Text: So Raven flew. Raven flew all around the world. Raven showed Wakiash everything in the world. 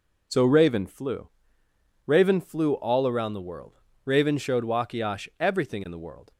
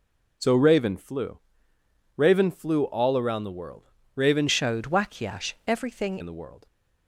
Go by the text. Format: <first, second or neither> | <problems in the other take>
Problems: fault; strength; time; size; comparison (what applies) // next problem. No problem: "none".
first | changes voice from "showed" to "everything"; from 4.4 to 6.1 s; 1.7 s long